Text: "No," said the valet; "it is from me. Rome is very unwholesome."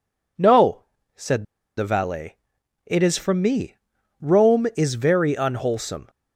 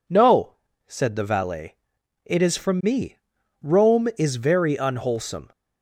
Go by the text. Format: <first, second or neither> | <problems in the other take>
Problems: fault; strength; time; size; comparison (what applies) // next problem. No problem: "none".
second | pauses between "said" and "the"; slight; at 1.4 s; 0.33 s long